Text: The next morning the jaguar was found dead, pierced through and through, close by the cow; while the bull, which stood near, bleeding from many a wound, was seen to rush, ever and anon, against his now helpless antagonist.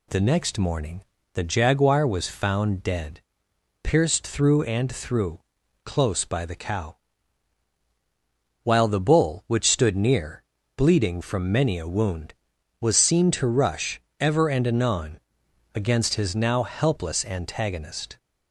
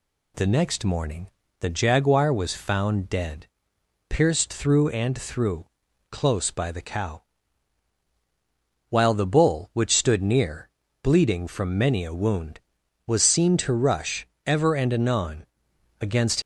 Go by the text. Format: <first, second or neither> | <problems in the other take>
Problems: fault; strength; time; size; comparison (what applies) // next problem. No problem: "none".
first | pauses between "morning" and "the"; slight; at 1.2 s; 0.30 s long; slight in the first // stops before "his now helpless antagonist"; at 16.4 s